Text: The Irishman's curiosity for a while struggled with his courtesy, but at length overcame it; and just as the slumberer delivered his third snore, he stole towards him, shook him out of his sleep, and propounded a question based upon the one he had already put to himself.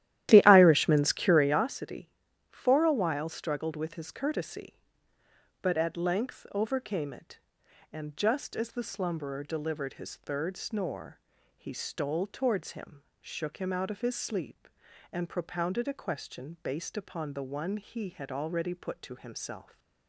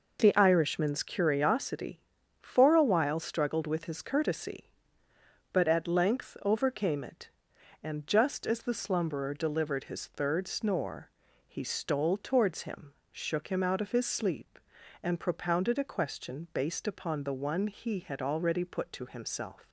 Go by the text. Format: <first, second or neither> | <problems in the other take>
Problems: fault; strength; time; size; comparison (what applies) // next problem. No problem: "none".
second | starts louder than the rest; strong; until 1.7 s; 13 dB